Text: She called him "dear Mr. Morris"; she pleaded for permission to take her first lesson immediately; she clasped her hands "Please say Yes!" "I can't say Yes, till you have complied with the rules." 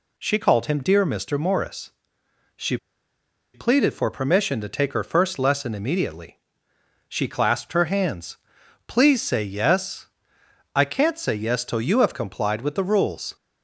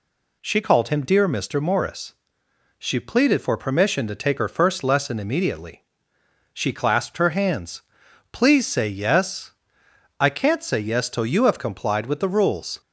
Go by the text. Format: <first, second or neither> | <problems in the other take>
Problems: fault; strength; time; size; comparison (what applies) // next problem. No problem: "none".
second | pauses between "she" and "pleaded"; noticeable; at 2.7 s; 0.77 s long // pauses between "hands" and "Please"; noticeable; at 8.3 s; 0.50 s long; noticeable in the second